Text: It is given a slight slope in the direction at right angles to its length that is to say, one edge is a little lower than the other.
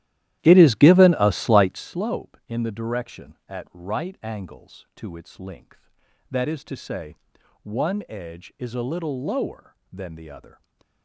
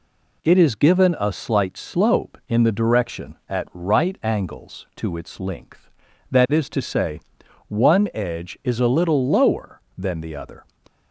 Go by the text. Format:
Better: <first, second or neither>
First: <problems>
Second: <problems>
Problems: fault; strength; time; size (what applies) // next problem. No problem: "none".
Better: second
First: starts louder than the rest; strong; until 2.0 s; 13.5 dB // stays silent after the last word; slight; from 10.5 s on; 0.5 s long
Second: none